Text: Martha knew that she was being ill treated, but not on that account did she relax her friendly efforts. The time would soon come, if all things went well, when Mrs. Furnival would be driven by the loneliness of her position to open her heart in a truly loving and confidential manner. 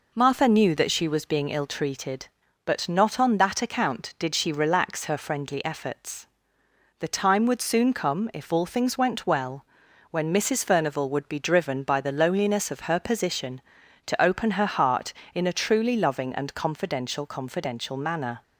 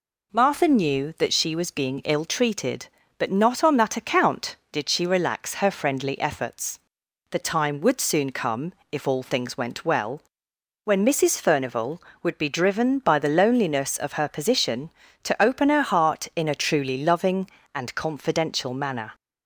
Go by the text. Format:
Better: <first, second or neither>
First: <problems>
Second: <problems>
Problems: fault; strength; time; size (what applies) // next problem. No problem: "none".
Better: second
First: says "confidential" twice; at 17.2 s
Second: none